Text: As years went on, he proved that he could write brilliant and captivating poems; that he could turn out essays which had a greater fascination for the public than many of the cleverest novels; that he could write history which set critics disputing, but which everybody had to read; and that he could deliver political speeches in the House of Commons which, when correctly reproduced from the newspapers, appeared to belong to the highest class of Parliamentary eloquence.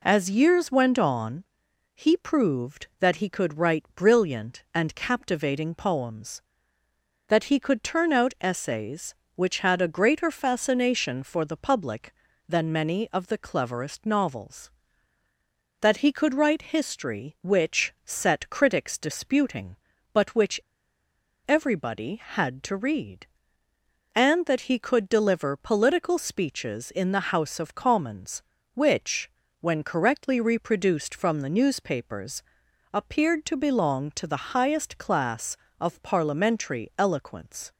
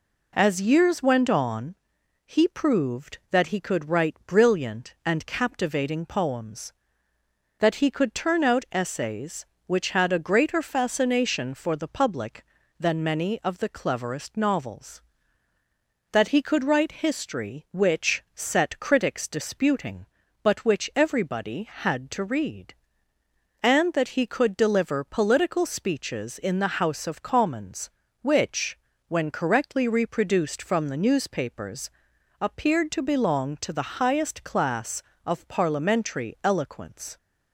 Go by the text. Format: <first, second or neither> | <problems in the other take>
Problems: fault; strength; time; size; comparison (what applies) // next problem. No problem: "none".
second | pauses between "which" and "everybody"; noticeable; at 20.5 s; 0.90 s long